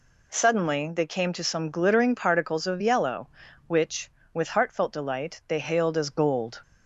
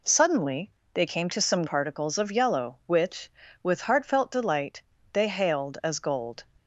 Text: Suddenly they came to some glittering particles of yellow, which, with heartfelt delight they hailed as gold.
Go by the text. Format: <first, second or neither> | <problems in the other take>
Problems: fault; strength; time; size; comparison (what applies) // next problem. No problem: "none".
first | pauses between "Suddenly" and "they"; slight; at 0.6 s; 0.26 s long // skips "glittering"; at 1.6 s // pauses between "delight" and "they"; slight; at 4.8 s; 0.30 s long